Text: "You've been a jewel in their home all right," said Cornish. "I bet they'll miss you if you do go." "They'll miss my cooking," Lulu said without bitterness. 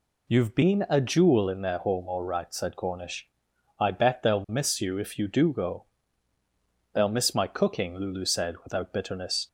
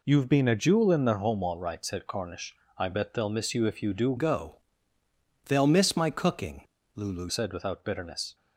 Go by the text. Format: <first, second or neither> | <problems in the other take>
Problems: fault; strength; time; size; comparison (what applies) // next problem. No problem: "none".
first | changes voice from "go" to "Lulu"; from 4.1 to 7.3 s; 3.2 s long